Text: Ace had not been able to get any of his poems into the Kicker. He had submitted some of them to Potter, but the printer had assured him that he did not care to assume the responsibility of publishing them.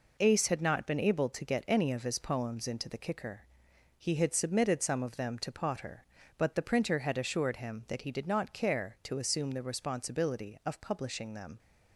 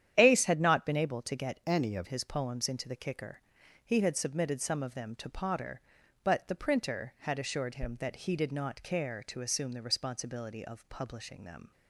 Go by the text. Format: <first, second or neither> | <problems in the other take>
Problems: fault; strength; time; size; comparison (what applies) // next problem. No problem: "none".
first | starts louder than the rest; strong; until 1.1 s; 10 dB // changes voice from "any" to "of"; from 1.6 to 2.0 s; 0.4 s long